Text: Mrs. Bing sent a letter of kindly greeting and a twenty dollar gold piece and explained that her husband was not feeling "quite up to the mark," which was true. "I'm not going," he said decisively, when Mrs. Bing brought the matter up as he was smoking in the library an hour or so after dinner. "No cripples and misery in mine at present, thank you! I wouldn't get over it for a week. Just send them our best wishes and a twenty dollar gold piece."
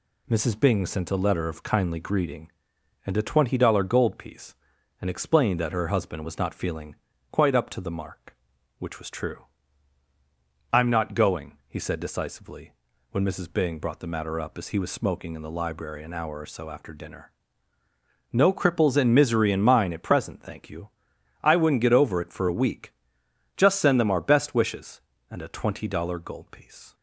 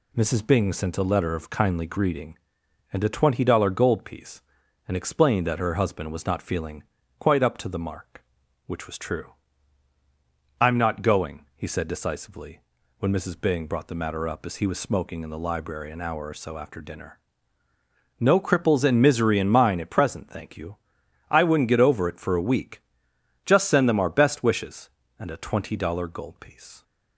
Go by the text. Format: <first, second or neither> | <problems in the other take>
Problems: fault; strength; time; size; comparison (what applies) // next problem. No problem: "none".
neither | pauses between "feeling" and "quite"; slight; the same in both